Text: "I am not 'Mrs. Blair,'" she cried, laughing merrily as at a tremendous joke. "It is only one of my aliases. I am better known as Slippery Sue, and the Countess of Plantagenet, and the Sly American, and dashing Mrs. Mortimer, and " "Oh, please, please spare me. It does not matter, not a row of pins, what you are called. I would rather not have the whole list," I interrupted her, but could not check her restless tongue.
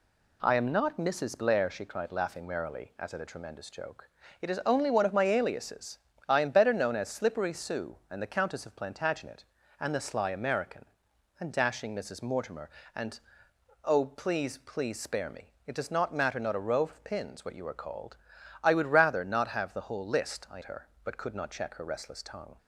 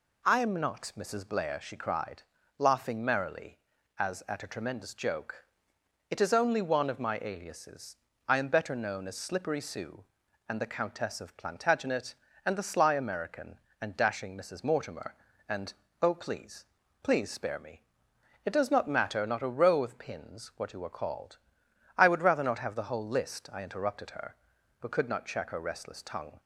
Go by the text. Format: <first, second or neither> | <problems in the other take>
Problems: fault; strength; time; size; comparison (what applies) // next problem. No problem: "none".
second | skips "interrupted"; at 20.6 s